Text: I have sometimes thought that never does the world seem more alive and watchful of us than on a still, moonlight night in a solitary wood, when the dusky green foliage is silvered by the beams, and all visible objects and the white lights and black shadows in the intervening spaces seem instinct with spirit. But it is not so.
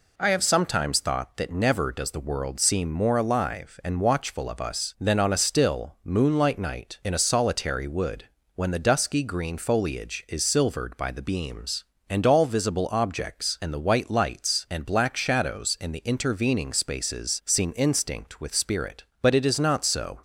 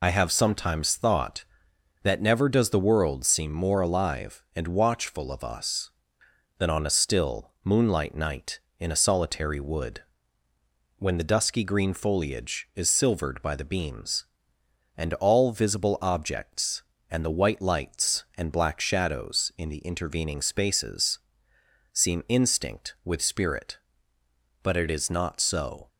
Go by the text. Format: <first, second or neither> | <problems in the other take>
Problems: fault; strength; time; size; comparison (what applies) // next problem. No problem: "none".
first | loses the start of "I"; at 0.0 s; 50 ms // pauses between "spaces" and "seem"; noticeable; at 21.1 s; 0.74 s long